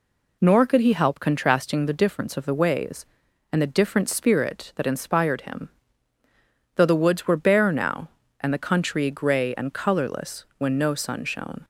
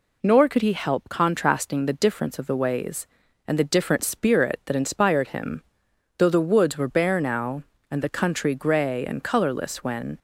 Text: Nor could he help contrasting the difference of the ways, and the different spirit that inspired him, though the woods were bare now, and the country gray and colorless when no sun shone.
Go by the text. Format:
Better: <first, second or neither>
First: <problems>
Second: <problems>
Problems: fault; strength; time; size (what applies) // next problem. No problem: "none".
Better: first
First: none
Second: stops before "no sun shone"; at 10.1 s